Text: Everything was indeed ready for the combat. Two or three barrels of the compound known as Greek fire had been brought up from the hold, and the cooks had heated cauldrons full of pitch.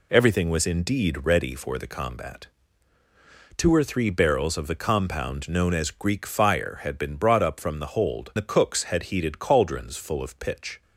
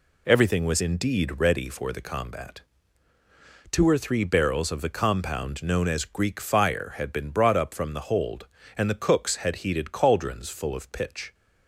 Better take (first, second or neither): second